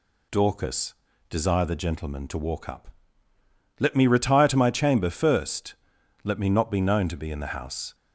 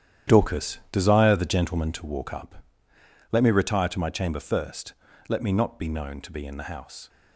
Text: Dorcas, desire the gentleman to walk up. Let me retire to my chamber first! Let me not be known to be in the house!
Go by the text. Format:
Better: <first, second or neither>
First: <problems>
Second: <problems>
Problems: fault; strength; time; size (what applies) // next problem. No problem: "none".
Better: first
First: none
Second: gets quieter; strong; throughout; 11 dB